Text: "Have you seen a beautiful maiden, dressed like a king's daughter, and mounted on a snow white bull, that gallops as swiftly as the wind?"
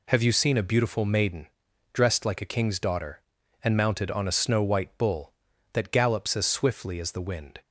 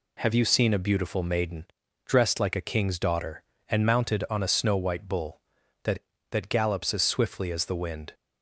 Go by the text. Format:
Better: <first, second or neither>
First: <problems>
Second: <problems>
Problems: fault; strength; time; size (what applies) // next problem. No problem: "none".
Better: first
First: none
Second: says "that" twice; at 6.3 s